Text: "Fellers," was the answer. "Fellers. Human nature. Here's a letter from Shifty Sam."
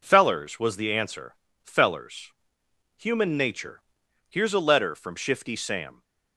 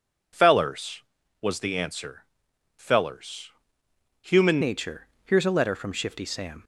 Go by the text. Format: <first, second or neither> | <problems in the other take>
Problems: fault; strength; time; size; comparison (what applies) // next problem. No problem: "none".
first | changes voice at "nature"; from 4.6 s on; 2.0 s long